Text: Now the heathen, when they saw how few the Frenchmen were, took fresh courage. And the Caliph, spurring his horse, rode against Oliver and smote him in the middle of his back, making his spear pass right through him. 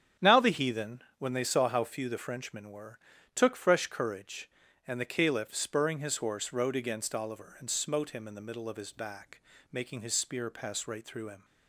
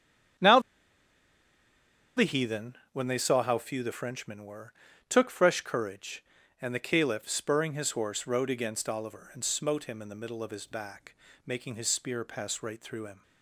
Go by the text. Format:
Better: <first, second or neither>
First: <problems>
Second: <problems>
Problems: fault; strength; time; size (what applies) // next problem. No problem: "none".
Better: first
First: starts louder than the rest; strong; until 1.3 s; 9 dB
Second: starts louder than the rest; strong; until 3.1 s; 9 dB // pauses between "Now" and "the"; strong; at 0.5 s; 1.5 s long